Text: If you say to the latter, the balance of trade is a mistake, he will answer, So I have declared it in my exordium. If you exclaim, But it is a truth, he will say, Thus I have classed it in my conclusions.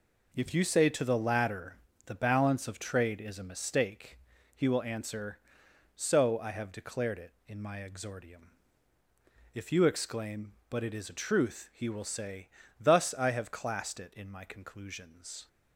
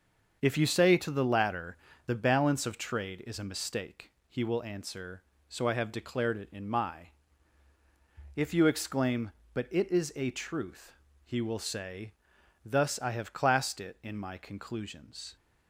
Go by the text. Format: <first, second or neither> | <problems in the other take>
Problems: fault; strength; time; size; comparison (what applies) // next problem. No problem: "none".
first | starts louder than the rest; until 1.4 s; 6.5 dB // skips "exordium"; at 7.7 s